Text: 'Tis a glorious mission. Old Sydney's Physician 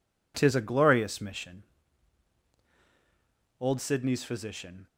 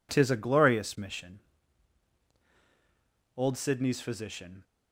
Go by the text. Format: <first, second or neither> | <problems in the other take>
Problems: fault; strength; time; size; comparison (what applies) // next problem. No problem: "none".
neither | none